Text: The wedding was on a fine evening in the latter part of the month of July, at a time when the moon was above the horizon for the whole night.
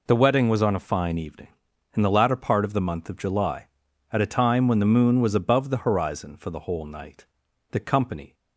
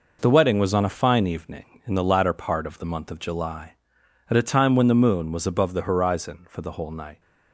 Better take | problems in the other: second | goes on to say "The company"; noticeable; from 7.7 s on; 0.62 s long

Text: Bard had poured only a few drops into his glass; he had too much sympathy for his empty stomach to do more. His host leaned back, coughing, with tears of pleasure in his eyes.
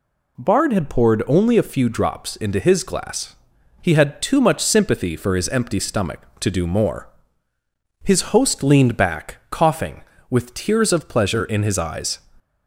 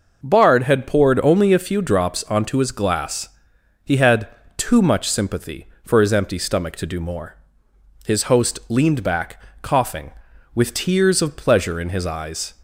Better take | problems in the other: first | says "onto" for "into"; at 2.2 s // pauses between "had" and "too"; slight; at 4.2 s; 0.28 s long

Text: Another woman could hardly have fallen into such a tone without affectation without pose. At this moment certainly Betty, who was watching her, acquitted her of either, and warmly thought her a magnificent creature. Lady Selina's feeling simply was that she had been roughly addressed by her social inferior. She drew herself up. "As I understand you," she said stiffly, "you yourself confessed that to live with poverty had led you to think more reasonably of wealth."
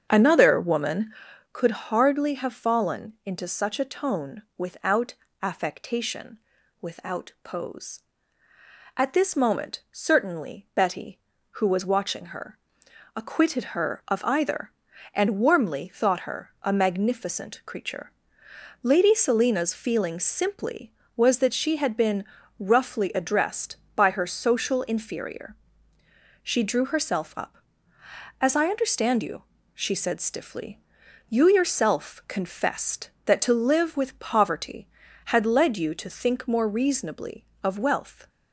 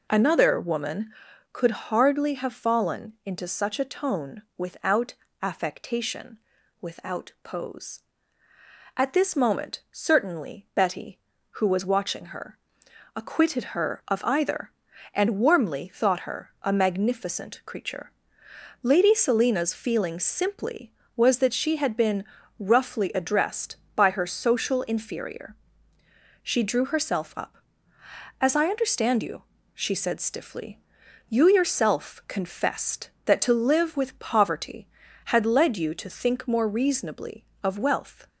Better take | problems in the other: second | starts louder than the rest; strong; until 1.5 s; 7.5 dB // pauses between "without" and "affectation"; slight; at 5.1 s; 0.28 s long; slight in the second // pauses between "affectation" and "without"; at 6.3 s; 0.44 s long; also in the second // pauses between "been" and "roughly"; slight; at 22.2 s; 0.36 s long; slight in the second

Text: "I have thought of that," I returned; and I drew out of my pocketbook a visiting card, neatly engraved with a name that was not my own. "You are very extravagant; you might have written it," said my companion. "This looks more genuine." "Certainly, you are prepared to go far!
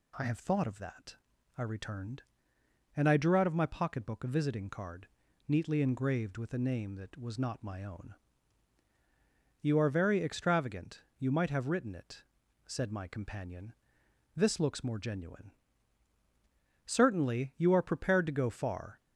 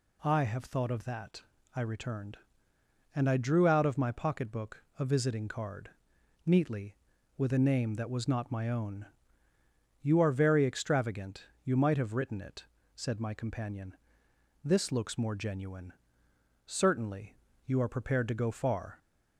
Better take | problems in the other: first | pauses between "pocketbook" and "a"; slight; at 4.8 s; 0.16 s long // skips "engraved"; at 7.1 s

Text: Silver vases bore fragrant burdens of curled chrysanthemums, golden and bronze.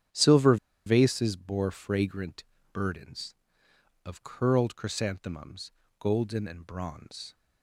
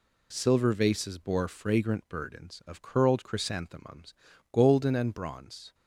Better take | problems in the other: second | starts louder than the rest; strong; until 1.4 s; 9 dB // pauses between "Silver" and "vases"; slight; at 0.5 s; 0.30 s long // pauses between "fragrant" and "burdens"; slight; at 2.4 s; 0.28 s long

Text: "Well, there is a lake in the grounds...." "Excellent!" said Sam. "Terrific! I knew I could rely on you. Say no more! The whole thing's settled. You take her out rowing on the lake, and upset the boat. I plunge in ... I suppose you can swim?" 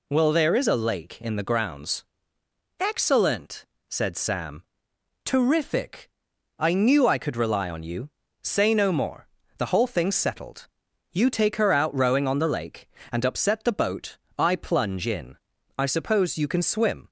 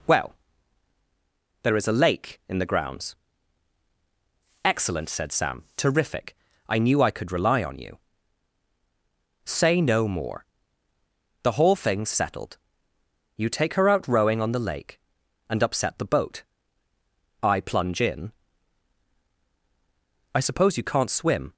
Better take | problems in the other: first | says "can't" for "can"; at 20.8 s

